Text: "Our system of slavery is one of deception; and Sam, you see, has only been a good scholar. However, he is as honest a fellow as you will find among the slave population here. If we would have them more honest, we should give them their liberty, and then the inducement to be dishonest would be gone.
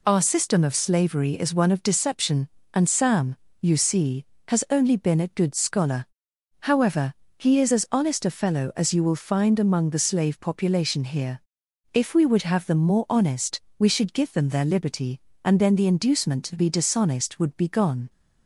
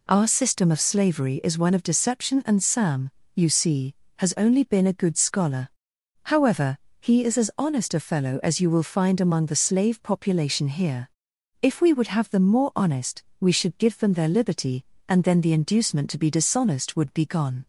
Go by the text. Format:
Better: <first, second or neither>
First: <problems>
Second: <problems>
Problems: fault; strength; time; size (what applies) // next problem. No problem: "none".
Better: neither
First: none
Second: none